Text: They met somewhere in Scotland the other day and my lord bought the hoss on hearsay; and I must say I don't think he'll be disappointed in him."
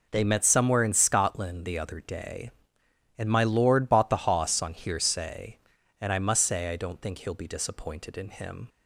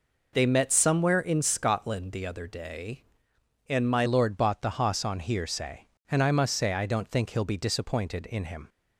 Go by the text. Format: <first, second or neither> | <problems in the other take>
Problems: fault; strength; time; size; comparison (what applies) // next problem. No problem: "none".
first | changes voice at "lord"; from 4.0 s on; 4.6 s long